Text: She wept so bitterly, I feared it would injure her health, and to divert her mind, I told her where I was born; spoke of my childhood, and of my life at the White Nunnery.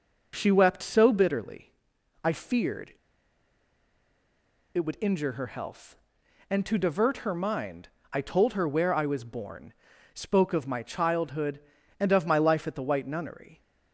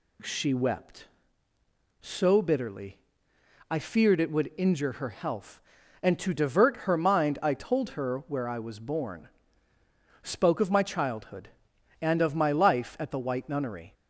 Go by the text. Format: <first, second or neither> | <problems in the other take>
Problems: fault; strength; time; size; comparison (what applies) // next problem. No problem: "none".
second | pauses between "feared" and "it"; strong; at 2.9 s; 1.8 s long